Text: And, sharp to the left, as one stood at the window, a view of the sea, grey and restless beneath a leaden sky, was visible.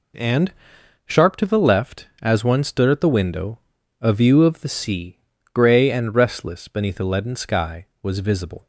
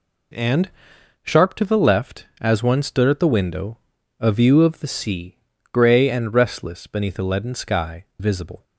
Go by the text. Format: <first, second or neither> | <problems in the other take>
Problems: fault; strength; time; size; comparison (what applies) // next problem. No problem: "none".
first | skips "was"; at 8.1 s